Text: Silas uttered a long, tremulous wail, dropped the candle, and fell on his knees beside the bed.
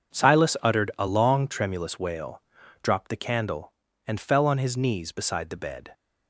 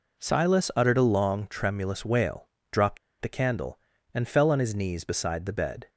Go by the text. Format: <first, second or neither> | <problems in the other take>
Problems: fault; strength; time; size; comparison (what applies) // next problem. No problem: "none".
first | pauses between "dropped" and "the"; slight; at 2.9 s; 0.23 s long